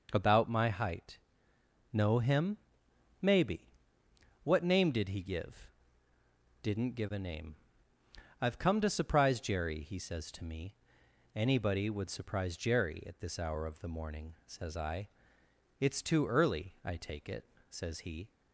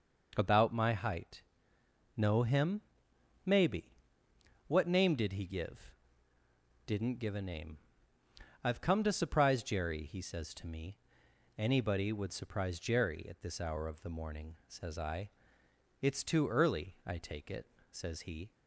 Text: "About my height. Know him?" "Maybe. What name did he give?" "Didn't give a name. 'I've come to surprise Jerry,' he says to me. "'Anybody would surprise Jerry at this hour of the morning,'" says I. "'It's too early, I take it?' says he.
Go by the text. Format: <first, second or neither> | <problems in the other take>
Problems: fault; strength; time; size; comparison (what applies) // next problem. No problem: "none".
neither | none